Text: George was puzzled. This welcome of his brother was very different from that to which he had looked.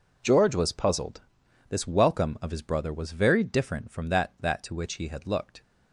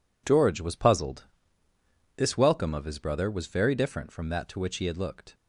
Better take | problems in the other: second | says "that" twice; at 4.3 s

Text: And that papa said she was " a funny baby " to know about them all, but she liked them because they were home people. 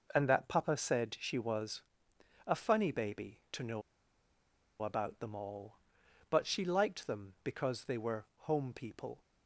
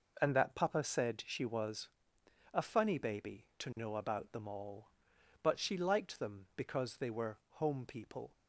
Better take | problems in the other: second | pauses between "know" and "about"; at 3.8 s; 1.0 s long

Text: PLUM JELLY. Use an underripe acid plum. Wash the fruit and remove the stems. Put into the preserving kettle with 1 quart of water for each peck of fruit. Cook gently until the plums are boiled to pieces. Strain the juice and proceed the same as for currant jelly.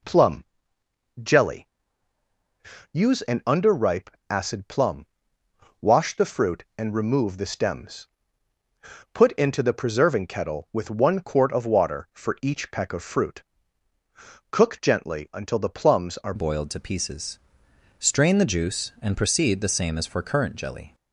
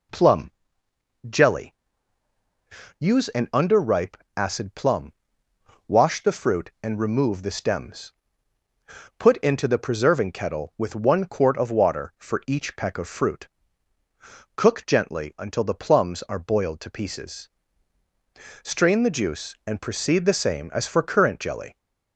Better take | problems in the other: second | pauses between "PLUM" and "JELLY"; noticeable; at 0.4 s; 0.78 s long; noticeable in the second // pauses between "underripe" and "acid"; slight; at 4.0 s; 0.20 s long; slight in the second // changes voice at "boiled"; from 16.3 s on; 4.6 s long

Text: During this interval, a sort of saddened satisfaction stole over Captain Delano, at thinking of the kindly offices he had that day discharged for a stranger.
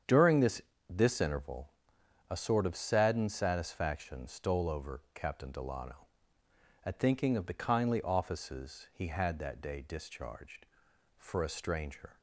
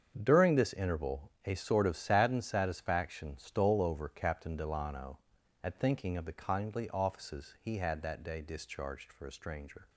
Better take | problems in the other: second | starts louder than the rest; strong; until 1.3 s; 8 dB; strong in the second // says "this" twice; at 0.8 s

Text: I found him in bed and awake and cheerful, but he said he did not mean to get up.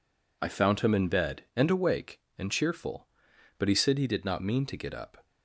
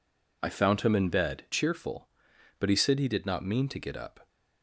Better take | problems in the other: first | skips "and awake and"; at 1.4 s

